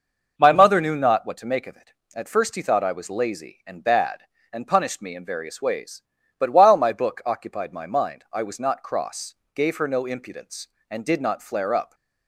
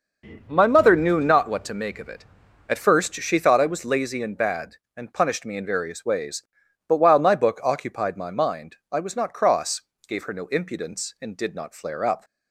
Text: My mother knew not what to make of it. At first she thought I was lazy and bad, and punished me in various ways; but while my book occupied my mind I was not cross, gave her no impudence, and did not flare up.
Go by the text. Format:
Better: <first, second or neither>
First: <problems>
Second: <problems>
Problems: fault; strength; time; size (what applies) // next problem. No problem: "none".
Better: second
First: says "he" for "she"; at 2.5 s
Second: none